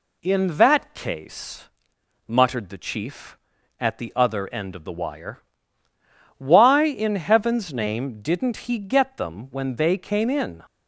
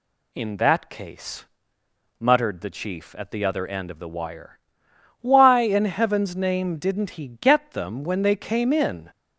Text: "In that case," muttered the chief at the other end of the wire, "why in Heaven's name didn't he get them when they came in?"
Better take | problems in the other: neither | none

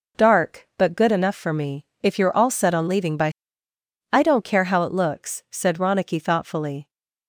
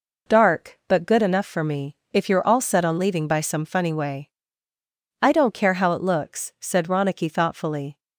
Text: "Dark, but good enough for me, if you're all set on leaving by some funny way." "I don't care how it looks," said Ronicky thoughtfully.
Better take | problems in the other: second | skips "some funny way"; at 3.7 s

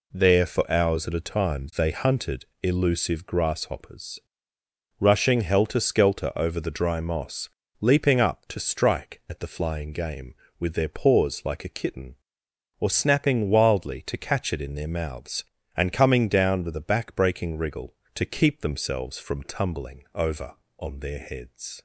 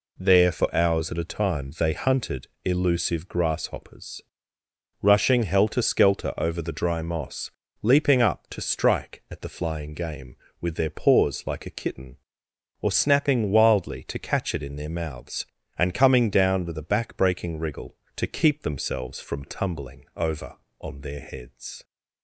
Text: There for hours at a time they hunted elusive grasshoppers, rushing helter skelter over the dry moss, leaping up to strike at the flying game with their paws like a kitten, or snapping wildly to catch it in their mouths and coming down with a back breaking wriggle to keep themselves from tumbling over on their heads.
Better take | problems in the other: neither | pauses between "hunted" and "elusive"; slight; the same in both

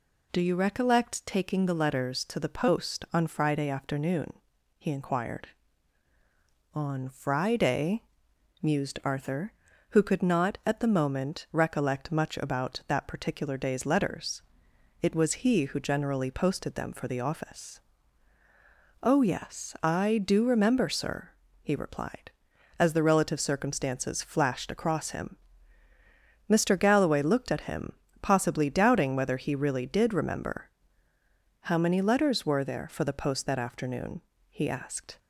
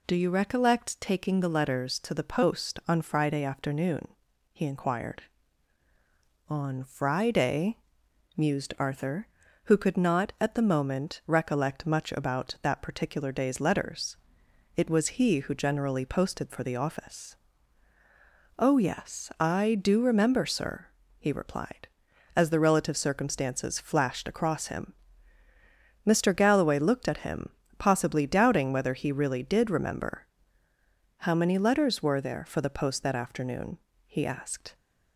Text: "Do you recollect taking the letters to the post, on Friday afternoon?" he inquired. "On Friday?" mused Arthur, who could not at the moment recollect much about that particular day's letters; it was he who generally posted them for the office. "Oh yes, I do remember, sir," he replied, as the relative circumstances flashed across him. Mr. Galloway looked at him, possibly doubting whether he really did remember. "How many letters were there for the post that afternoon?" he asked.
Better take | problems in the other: first | skips "them"; at 16.4 s

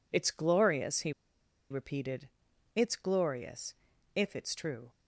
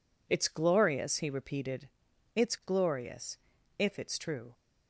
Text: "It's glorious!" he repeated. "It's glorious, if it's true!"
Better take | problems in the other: second | pauses between "he" and "repeated"; noticeable; at 1.1 s; 0.57 s long

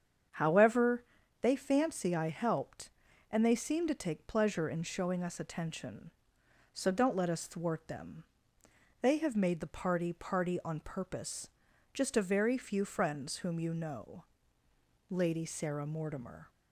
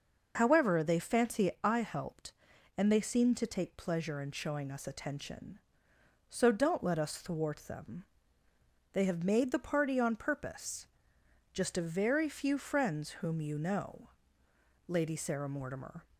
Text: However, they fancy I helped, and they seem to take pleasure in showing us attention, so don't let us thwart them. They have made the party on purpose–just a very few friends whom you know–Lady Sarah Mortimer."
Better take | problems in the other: second | starts louder than the rest; strong; until 1.7 s; 7.5 dB // says "party" twice; at 10.1 s

